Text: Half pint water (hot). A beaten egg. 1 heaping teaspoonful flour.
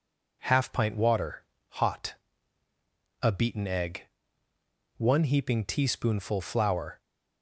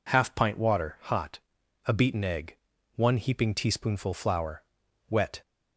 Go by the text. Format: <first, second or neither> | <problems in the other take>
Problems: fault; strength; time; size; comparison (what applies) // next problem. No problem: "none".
first | goes on to say "Wet"; slight; from 5.0 s on; 0.32 s long